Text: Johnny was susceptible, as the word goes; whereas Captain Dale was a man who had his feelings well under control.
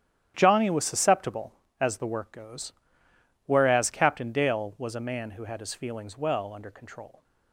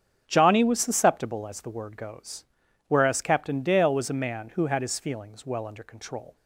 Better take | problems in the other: second | starts louder than the rest; strong; until 1.3 s; 10 dB; strong in the second // says "work" for "word"; at 2.0 s

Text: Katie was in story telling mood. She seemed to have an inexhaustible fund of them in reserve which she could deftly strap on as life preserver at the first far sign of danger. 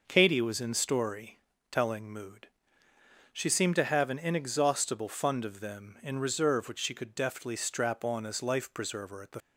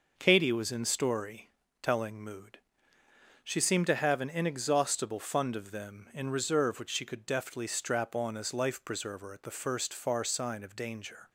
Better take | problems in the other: second | pauses between "story" and "telling"; slight; at 1.3 s; 0.32 s long; slight in the second // stops before "first far sign of danger"; at 9.4 s

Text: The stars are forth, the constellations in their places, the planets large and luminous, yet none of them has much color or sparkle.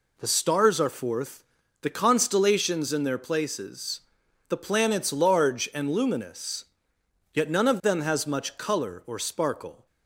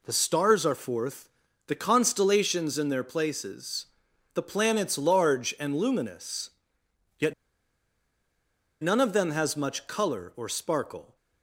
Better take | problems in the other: first | pauses between "yet" and "none"; strong; at 7.3 s; 1.4 s long

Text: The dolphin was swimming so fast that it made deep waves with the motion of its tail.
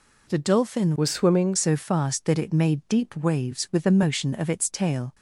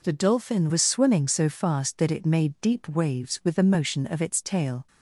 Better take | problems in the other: second | changes voice from "was" to "swimming"; from 0.9 to 1.5 s; 0.6 s long

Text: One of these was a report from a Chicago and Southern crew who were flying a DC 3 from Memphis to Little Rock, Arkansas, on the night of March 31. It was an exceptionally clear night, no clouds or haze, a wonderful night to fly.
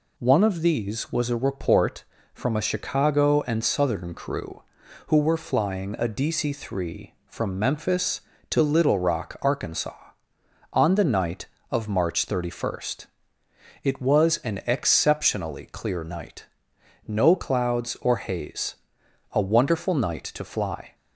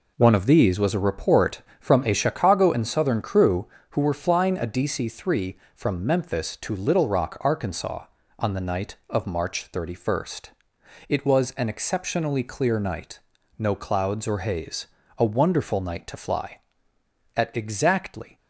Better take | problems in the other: first | goes on to say "At exactly"; noticeable; from 17.3 s on; 1.0 s long

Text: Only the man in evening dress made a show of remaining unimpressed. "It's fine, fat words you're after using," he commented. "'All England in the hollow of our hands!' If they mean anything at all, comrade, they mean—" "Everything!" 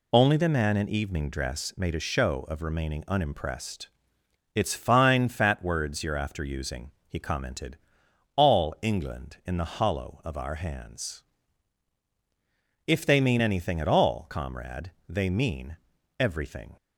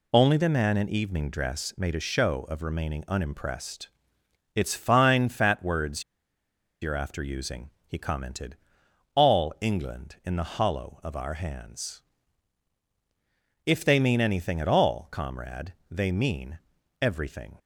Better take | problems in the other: first | pauses between "words" and "you're"; noticeable; at 6.0 s; 0.80 s long

